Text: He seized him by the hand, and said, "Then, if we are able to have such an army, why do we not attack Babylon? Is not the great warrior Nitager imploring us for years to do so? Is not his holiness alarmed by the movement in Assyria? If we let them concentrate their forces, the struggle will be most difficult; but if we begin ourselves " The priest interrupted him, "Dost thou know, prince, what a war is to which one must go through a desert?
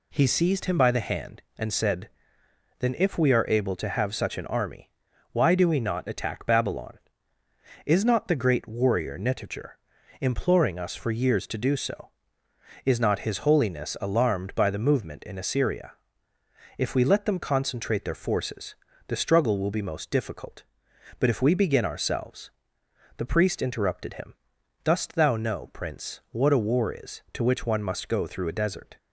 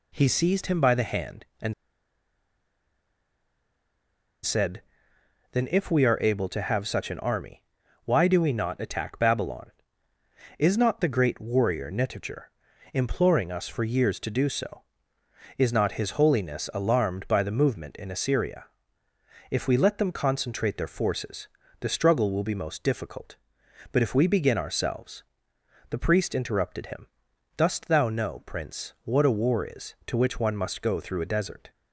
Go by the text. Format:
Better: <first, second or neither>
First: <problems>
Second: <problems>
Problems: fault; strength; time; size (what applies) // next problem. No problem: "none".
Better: first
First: pauses between "Nitager" and "imploring"; at 9.7 s; 0.42 s long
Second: pauses between "and" and "said"; strong; at 1.7 s; 2.7 s long // pauses between "Nitager" and "imploring"; at 12.5 s; 0.42 s long